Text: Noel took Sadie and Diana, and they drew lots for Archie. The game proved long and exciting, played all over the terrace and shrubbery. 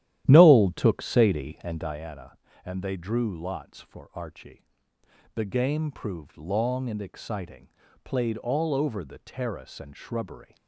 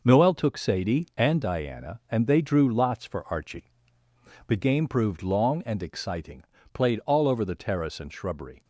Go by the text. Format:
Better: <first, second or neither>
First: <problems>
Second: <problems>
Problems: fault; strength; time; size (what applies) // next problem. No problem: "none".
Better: second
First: starts louder than the rest; strong; until 2.0 s; 12 dB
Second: none